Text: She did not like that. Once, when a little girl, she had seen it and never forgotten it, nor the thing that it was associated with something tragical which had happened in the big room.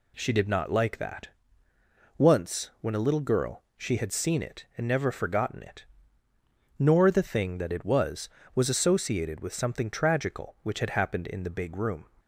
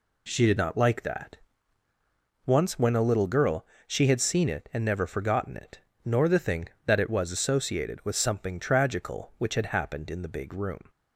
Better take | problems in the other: second | says "was" twice; at 8.5 s

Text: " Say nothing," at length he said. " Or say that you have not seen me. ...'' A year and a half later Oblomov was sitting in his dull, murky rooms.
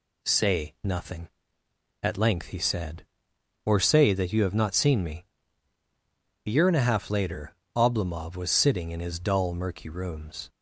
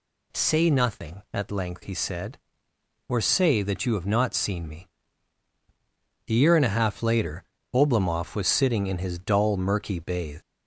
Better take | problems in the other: first | pauses between "later" and "Oblomov"; slight; at 7.4 s; 0.30 s long; slight in the first // says "bathe" for "rooms"; at 9.9 s

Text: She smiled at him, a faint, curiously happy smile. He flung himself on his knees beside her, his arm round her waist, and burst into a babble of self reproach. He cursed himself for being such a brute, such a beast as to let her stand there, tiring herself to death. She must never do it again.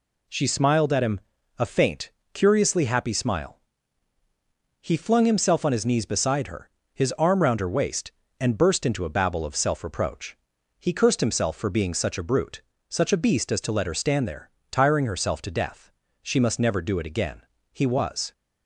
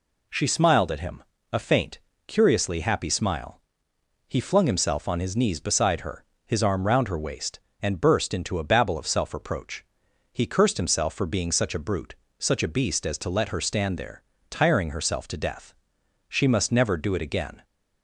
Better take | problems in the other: second | goes on to say "He was"; from 17.7 s on; 0.60 s long

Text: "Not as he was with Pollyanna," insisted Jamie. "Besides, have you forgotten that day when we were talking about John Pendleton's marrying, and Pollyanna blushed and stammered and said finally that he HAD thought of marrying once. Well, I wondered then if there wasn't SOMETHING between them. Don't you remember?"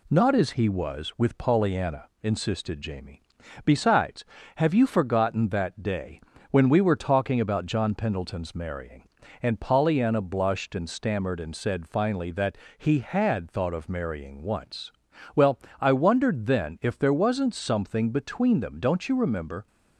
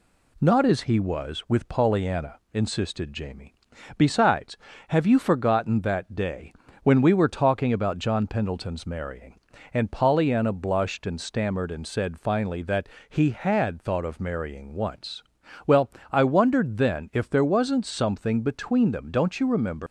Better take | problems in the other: first | pauses between "day" and "when"; slight; at 6.5 s; 0.30 s long; slight in the first // pauses between "that" and "he"; slight; at 12.8 s; 0.20 s long; slight in the first // leaves "remember" unfinished; at 19.8 s; 115 ms

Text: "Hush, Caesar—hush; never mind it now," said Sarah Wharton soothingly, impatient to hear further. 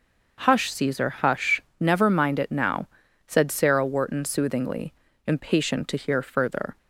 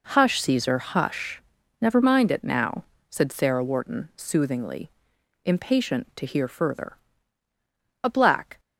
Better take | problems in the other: first | goes on to say "A black"; from 8.0 s on; 0.56 s long

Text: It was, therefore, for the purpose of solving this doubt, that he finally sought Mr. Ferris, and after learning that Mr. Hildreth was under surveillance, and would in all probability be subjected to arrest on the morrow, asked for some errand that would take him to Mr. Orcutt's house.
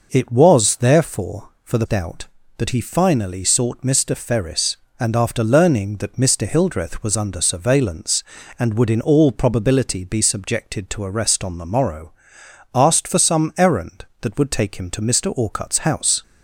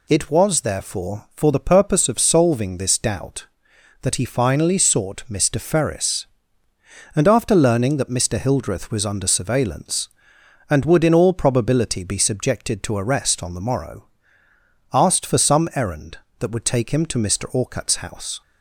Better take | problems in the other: second | skips "purpose of solving this"; at 1.8 s

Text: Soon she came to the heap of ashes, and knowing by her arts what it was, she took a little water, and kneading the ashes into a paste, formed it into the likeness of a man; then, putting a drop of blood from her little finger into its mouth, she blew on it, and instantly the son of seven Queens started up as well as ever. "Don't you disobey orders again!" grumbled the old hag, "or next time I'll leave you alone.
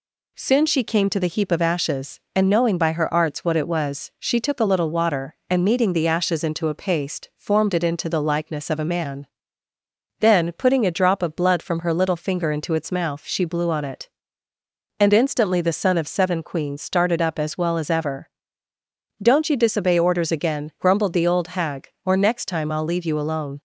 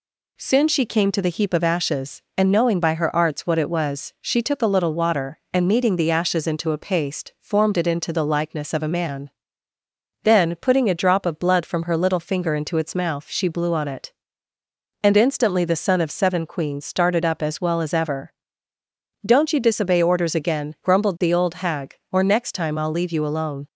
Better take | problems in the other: neither | none

